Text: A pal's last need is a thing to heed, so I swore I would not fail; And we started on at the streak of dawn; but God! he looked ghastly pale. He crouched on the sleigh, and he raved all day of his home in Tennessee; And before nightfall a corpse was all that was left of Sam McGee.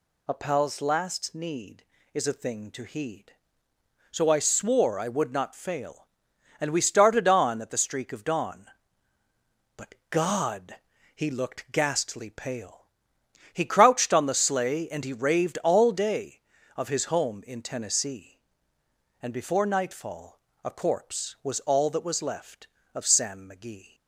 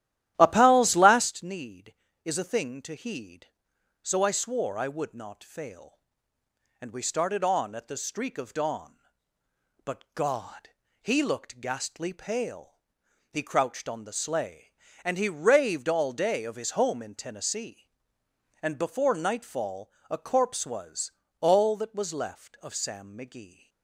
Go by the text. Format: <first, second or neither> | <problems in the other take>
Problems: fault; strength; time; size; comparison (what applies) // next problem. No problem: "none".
first | starts louder than the rest; strong; until 1.3 s; 12.5 dB // pauses between "nightfall" and "a"; slight; at 19.8 s; 0.22 s long; slight in the first // pauses between "was" and "all"; slight; at 21.1 s; 0.26 s long